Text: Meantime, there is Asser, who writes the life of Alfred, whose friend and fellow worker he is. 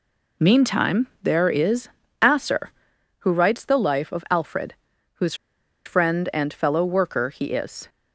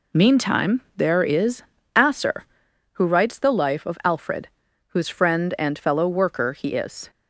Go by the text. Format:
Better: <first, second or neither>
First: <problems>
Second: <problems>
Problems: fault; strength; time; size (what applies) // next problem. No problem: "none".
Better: second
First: pauses between "is" and "Asser"; slight; at 1.8 s; 0.32 s long // pauses between "whose" and "friend"; noticeable; at 5.3 s; 0.51 s long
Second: pauses between "is" and "Asser"; slight; at 1.6 s; 0.32 s long